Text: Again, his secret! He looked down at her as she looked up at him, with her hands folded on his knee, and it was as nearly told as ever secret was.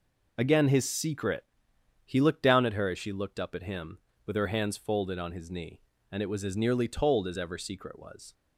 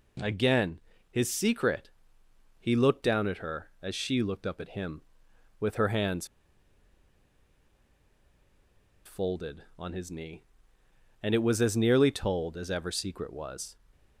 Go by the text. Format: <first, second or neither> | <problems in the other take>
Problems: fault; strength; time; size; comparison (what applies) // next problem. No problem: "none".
first | pauses between "hands" and "folded"; strong; at 6.2 s; 2.7 s long